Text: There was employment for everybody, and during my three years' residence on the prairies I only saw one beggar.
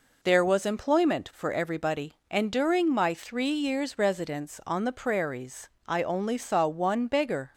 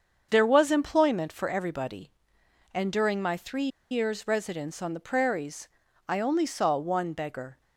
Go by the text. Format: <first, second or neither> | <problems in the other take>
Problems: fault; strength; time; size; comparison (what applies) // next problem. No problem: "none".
first | starts louder than the rest; until 1.3 s; 7 dB // pauses between "three" and "years"; slight; at 3.6 s; 0.23 s long // pauses between "prairies" and "I"; at 5.6 s; 0.40 s long; slight in the first